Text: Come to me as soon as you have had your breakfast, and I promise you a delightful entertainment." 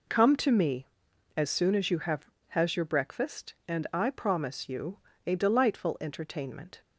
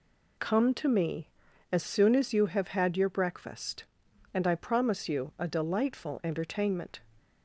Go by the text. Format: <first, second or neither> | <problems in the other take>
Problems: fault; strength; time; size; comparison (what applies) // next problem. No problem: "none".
second | says "has" for "had"; at 2.5 s // pauses between "you" and "a"; slight; at 4.9 s; 0.30 s long